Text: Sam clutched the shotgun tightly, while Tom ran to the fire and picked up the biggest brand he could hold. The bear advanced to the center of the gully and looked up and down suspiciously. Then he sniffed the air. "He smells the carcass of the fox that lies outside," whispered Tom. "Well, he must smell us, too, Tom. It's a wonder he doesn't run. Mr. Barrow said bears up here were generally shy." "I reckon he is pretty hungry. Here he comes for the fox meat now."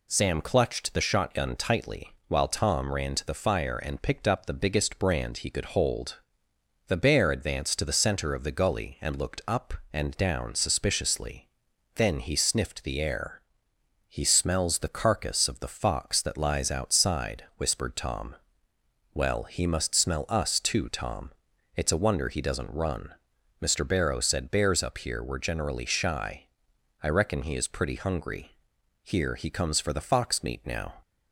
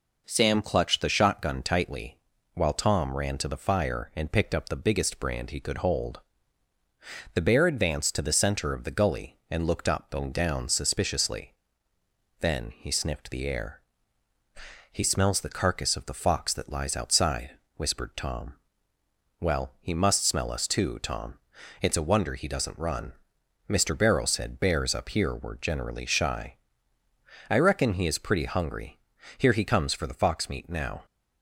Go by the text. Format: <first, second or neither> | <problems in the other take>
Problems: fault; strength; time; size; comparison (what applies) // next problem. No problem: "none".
neither | none